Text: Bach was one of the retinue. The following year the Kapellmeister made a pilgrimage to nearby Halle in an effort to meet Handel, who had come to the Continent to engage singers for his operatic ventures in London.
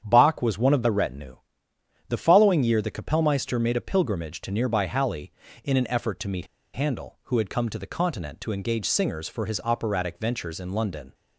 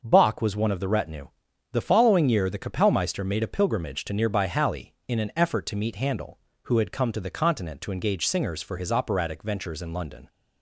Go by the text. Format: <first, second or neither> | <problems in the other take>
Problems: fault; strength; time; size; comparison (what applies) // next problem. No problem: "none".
second | starts louder than the rest; strong; until 1.0 s; 8.5 dB; noticeable in the second // pauses between "meet" and "Handel"; slight; at 6.4 s; 0.27 s long